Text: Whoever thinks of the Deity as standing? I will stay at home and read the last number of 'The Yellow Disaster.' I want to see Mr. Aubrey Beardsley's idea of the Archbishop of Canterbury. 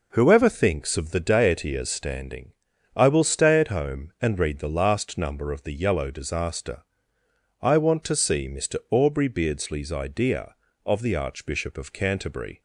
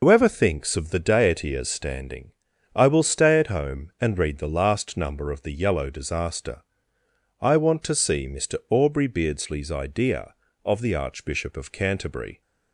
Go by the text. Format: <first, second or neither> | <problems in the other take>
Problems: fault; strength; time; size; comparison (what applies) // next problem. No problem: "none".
first | loses the start of "Whoever"; at 0.0 s; 105 ms